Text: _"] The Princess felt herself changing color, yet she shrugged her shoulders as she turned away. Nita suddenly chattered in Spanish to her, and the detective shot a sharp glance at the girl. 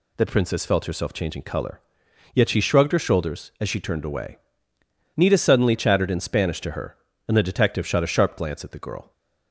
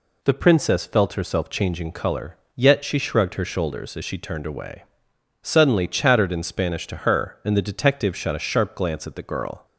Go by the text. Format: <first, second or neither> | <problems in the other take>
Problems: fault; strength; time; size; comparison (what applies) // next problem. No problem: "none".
first | skips "Nita"; at 5.1 s